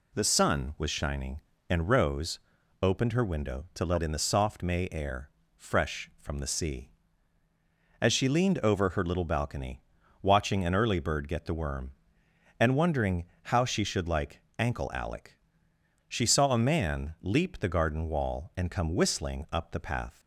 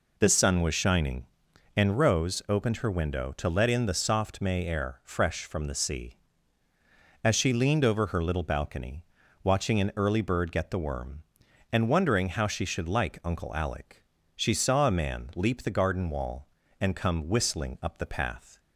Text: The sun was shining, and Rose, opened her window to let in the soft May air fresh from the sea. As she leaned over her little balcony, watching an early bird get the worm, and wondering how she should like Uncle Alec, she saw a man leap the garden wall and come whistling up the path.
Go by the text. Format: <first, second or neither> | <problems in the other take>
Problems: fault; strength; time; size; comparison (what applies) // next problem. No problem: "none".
second | pauses between "air" and "fresh"; slight; at 5.2 s; 0.26 s long // pauses between "wondering" and "how"; slight; at 13.2 s; 0.20 s long // says "Ankle" for "Uncle"; at 14.5 s